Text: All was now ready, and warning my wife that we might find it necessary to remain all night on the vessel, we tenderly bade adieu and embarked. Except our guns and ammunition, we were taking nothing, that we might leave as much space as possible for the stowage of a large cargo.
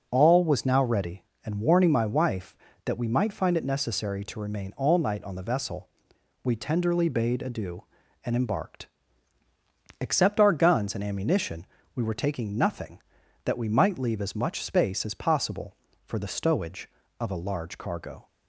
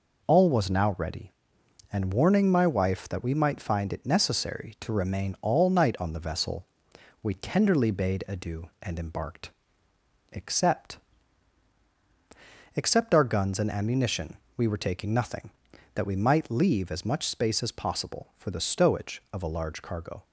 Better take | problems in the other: first | says "Except" twice; at 12.7 s

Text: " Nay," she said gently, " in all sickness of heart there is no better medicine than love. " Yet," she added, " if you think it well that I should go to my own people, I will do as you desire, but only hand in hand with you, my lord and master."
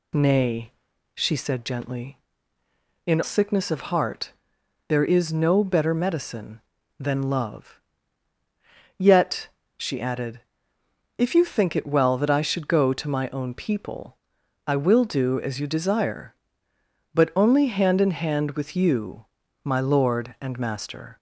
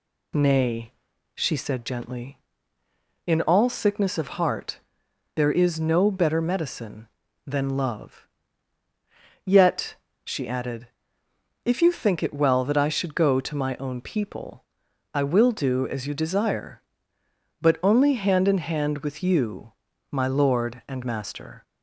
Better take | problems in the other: second | skips "all"; at 3.2 s // pauses between "heart" and "there"; noticeable; at 4.3 s; 0.56 s long; noticeable in the second

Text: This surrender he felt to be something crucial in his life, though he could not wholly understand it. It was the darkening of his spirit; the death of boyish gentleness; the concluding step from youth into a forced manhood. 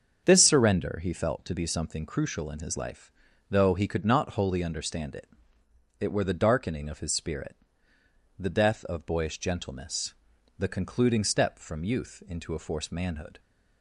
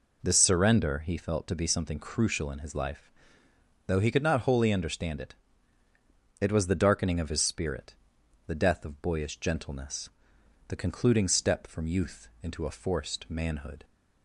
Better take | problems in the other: second | starts louder than the rest; until 1.2 s; 7 dB // says "were" for "was"; at 6.1 s

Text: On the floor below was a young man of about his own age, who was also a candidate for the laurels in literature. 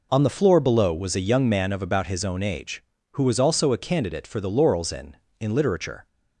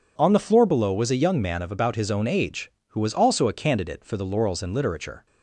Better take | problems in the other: second | says "in" twice; at 5.3 s

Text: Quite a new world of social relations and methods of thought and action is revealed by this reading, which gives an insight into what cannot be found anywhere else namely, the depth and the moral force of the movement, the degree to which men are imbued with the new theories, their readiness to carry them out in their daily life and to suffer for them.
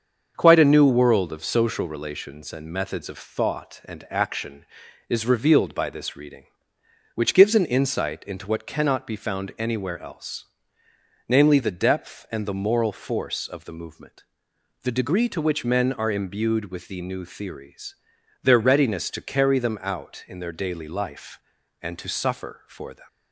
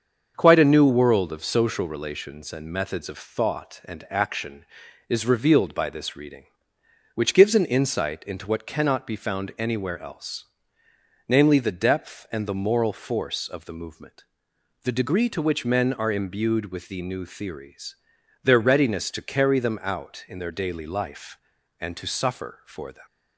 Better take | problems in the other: neither | starts louder than the rest; the same in both // pauses between "else" and "namely"; noticeable; the same in both

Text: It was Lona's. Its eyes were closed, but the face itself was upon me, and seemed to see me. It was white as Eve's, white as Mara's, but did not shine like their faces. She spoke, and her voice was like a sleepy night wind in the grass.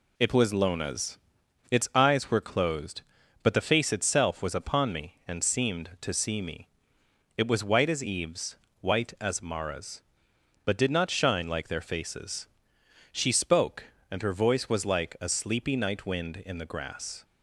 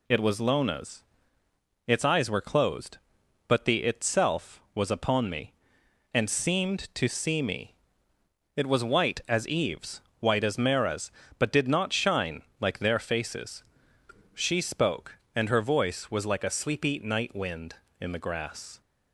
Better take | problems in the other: first | skips "face"; at 3.8 s // pauses between "shine" and "like"; slight; at 12.4 s; 0.16 s long

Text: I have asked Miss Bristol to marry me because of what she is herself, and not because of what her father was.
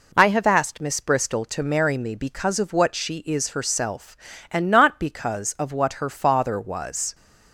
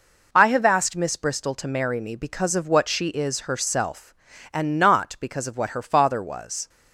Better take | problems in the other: neither | none

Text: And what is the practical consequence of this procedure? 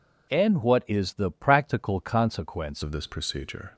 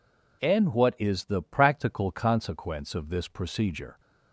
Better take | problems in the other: second | changes voice at "of"; from 2.8 s on; 0.9 s long

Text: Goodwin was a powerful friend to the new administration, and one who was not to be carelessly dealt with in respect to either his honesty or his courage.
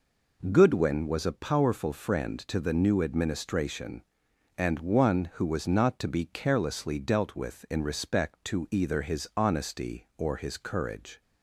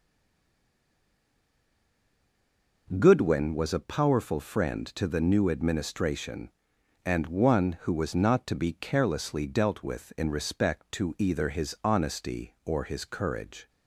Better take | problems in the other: first | stays silent before the first word; strong; until 2.8 s; 2.8 s long

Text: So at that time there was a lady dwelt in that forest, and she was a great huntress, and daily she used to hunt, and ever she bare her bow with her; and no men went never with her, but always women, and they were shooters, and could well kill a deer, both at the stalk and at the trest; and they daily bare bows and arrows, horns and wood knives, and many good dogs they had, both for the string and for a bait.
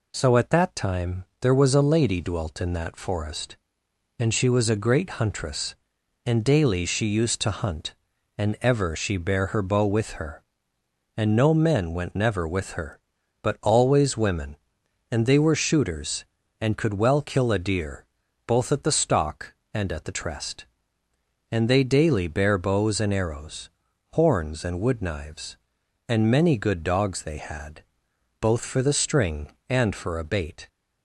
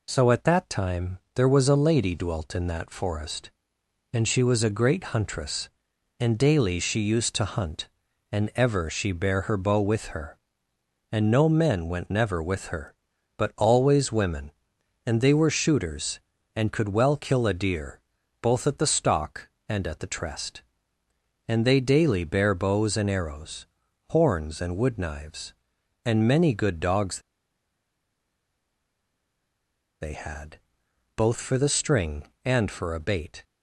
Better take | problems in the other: first | pauses between "time" and "there"; slight; at 1.1 s; 0.18 s long; slight in the first // pauses between "dogs" and "they"; strong; at 27.2 s; 2.8 s long

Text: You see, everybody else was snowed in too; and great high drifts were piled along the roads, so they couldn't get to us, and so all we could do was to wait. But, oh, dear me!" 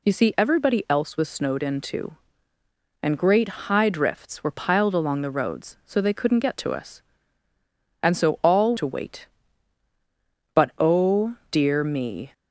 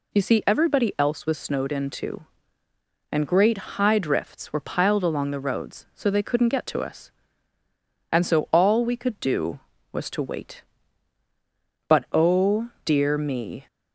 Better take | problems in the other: second | skips "we could do was"; at 8.7 s

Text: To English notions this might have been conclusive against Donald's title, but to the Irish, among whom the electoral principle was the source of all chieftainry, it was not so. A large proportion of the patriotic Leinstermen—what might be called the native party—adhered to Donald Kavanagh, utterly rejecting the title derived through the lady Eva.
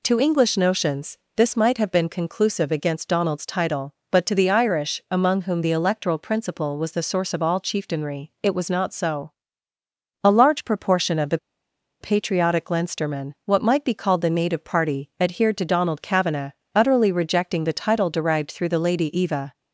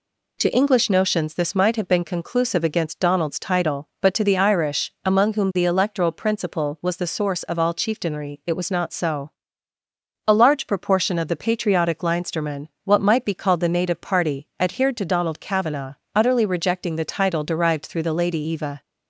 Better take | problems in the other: second | pauses between "notions" and "this"; slight; at 1.1 s; 0.18 s long // pauses between "the" and "patriotic"; noticeable; at 11.3 s; 0.62 s long

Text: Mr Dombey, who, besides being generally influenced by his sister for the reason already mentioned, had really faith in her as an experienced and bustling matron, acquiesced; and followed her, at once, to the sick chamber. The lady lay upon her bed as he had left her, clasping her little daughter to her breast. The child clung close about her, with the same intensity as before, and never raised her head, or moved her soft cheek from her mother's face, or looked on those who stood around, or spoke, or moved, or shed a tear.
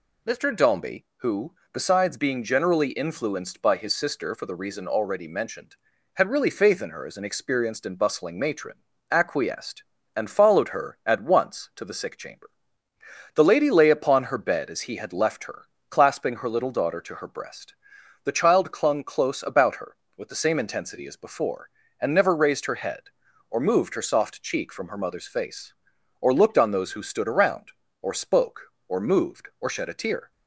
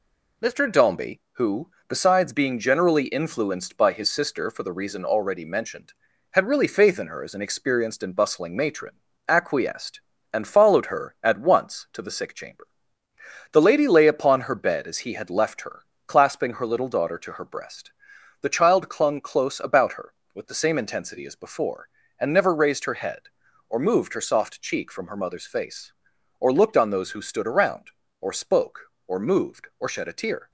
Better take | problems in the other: first | gets quieter; throughout; 3.5 dB

